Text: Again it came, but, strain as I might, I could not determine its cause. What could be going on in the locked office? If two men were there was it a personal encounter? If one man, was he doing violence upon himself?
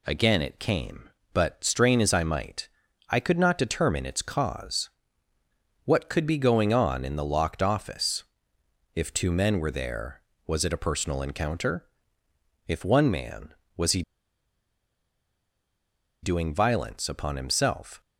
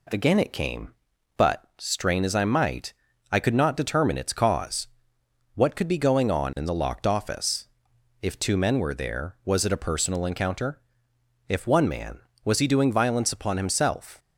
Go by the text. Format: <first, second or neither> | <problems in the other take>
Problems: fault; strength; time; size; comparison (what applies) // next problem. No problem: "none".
second | pauses between "he" and "doing"; strong; at 14.0 s; 2.2 s long